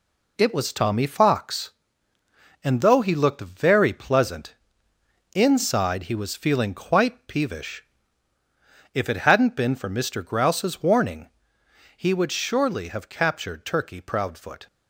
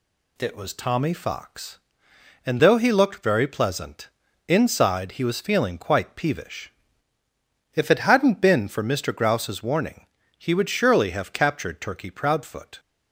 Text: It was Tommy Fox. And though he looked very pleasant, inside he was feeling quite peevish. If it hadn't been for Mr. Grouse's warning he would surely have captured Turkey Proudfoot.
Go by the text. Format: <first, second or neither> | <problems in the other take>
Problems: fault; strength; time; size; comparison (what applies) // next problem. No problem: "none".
second | gets quieter; throughout; 6.5 dB // pauses between "warning" and "he"; noticeable; at 11.2 s; 0.69 s long; slight in the second